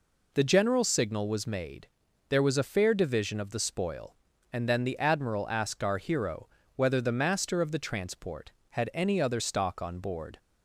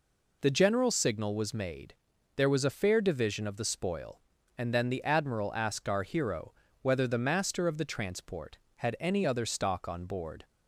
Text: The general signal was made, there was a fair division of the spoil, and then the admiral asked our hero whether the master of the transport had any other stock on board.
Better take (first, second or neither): neither